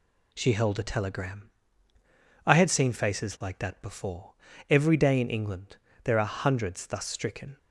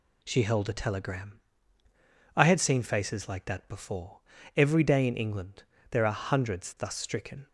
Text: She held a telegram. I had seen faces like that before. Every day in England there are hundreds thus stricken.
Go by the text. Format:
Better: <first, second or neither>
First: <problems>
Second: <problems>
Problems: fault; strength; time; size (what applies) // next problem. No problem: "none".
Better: neither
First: pauses between "England" and "there"; slight; at 5.7 s; 0.26 s long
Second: pauses between "England" and "there"; slight; at 5.6 s; 0.26 s long